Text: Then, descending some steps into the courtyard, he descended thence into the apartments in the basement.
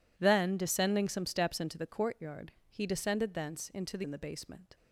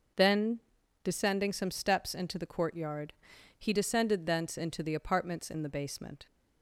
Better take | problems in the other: second | skips "apartments"; at 4.0 s

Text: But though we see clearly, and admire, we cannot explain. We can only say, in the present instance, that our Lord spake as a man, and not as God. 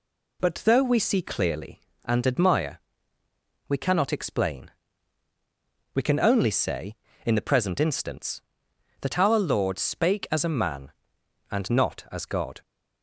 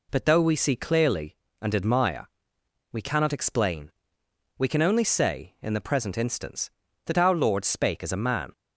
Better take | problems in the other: first | stops before "and not as God"; at 8.5 s

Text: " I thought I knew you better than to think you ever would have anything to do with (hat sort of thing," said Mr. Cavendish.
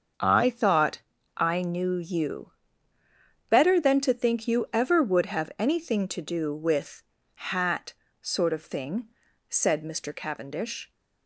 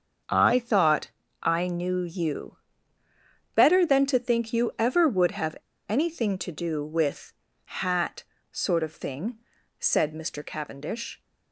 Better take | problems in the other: first | starts louder than the rest; until 1.5 s; 6.5 dB; also in the first // pauses between "thought" and "I"; slight; at 1.0 s; 0.32 s long; slight in the first // pauses between "you" and "better"; at 2.5 s; 1.0 s long; also in the first // pauses between "have" and "anything"; slight; at 5.5 s; 0.32 s long // pauses between "hat" and "sort"; slight; at 8.2 s; 0.26 s long; slight in the first

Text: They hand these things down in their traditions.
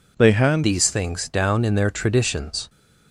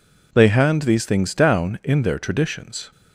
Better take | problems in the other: second | changes voice at "these"; from 0.6 s on; 2.0 s long

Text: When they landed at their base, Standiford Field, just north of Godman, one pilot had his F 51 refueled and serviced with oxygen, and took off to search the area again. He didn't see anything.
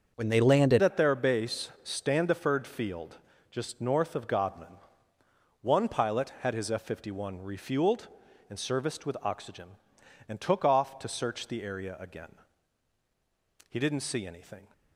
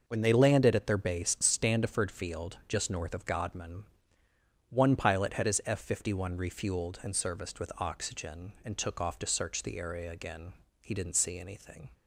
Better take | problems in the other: second | starts louder than the rest; until 1.1 s; 6.5 dB // changes voice at "at"; from 0.8 s on; 13.8 s long

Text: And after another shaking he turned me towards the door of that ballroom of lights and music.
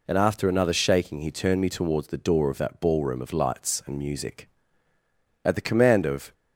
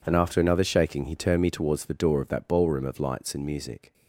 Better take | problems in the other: second | goes on to say "At the command of"; noticeable; from 5.4 s on; 0.88 s long

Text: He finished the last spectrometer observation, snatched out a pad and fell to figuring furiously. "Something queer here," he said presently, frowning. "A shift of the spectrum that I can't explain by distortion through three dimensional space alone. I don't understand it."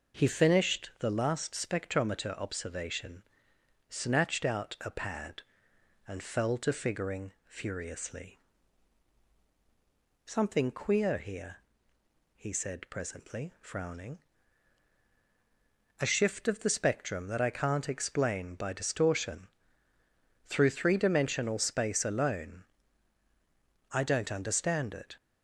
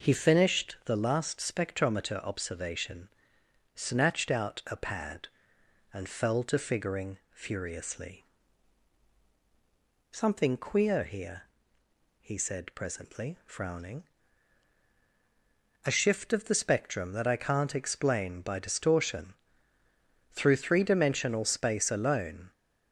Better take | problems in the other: first | pauses between "distortion" and "through"; noticeable; at 19.3 s; 0.96 s long; noticeable in the first // stops before "I don't understand it"; at 22.5 s

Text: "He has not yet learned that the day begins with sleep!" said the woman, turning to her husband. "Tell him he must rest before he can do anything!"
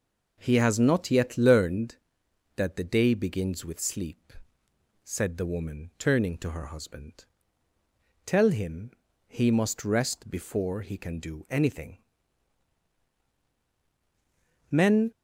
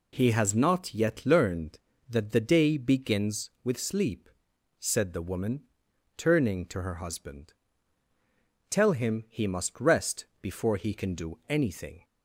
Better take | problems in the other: second | pauses between "him" and "he"; slight; at 8.9 s; 0.36 s long // goes on to say "Men"; slight; from 14.7 s on; 0.40 s long

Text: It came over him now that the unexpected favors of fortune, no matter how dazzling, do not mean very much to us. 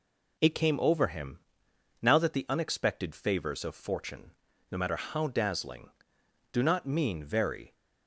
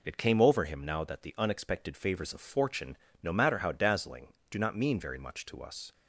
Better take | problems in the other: second | pauses between "him" and "now"; noticeable; at 1.3 s; 0.62 s long // stops before "much to us"; at 7.7 s

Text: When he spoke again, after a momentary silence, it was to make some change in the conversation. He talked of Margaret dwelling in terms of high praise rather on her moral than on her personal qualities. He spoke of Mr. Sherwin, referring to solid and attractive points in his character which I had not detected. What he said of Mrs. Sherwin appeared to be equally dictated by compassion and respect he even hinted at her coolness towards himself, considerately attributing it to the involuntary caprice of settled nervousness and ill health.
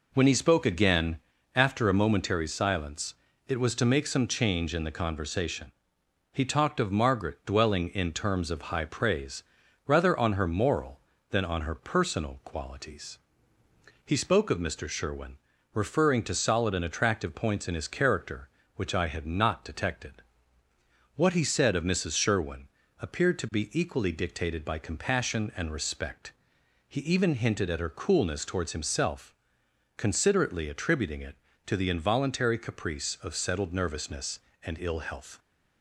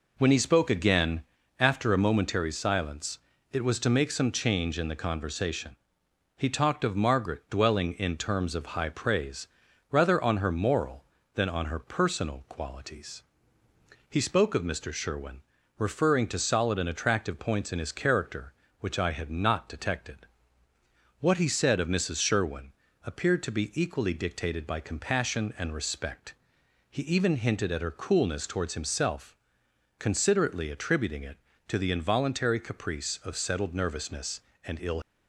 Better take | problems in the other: first | pauses between "praise" and "rather"; at 9.4 s; 0.44 s long; also in the first // pauses between "Sherwin" and "appeared"; slight; at 22.7 s; 0.32 s long; slight in the first // pauses between "respect" and "he"; noticeable; at 26.3 s; 0.56 s long; noticeable in the first // stops before "health"; at 35.0 s

